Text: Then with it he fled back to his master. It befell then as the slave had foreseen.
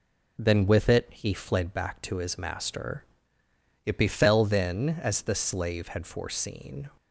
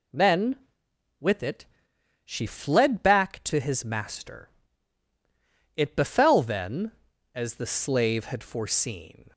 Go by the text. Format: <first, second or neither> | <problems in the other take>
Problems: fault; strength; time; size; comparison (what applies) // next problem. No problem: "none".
first | says "she" for "he"; at 2.2 s